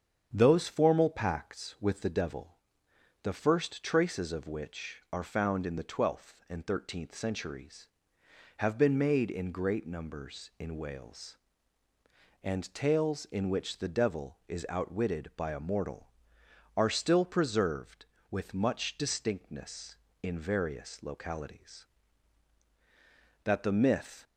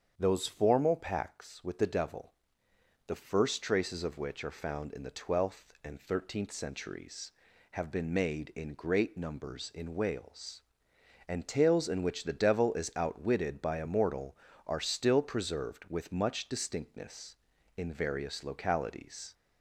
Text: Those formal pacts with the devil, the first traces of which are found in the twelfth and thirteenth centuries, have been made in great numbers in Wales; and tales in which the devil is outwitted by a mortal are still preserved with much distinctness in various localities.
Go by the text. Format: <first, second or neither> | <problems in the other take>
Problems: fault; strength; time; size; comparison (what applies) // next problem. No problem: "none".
second | starts louder than the rest; strong; until 1.3 s; 8 dB; strong in the second // goes on to say "That the myth"; noticeable; from 23.4 s on; 0.80 s long